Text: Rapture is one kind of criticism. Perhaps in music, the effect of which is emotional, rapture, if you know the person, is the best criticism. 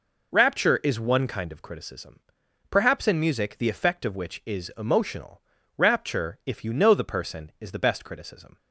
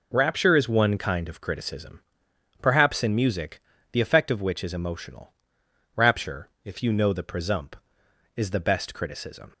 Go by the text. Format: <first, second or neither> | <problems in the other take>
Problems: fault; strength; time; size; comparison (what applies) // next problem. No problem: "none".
first | says "presump" for "person"; at 7.2 s